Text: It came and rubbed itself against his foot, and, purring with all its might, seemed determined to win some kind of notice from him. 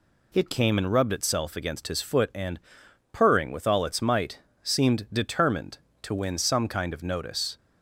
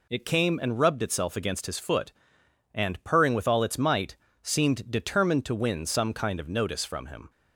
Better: second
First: stops before "from him"; at 7.5 s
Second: none

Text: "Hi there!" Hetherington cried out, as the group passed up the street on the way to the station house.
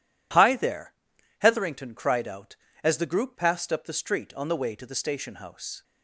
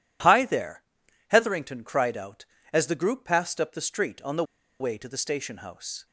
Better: first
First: none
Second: pauses between "the" and "way"; at 4.4 s; 0.36 s long

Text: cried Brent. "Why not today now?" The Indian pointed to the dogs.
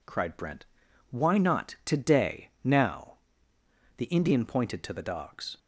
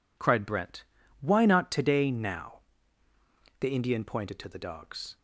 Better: neither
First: none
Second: none

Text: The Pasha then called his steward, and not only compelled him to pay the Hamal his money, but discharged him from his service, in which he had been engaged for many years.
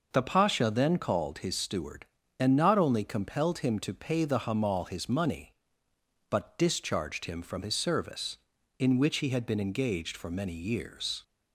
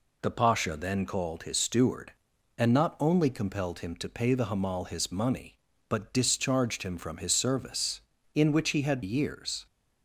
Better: first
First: none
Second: skips "been engaged for many"; at 9.0 s

